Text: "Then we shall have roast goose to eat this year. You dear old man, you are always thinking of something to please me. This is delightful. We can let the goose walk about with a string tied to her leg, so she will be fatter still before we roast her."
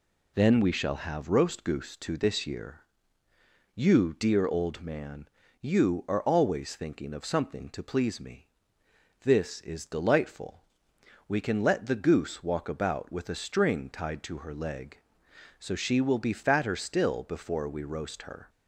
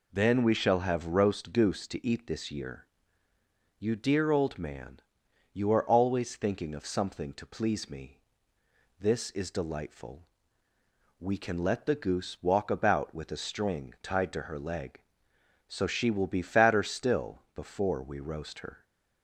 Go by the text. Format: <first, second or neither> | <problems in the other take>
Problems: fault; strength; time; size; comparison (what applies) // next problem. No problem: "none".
second | skips "eat"; at 2.1 s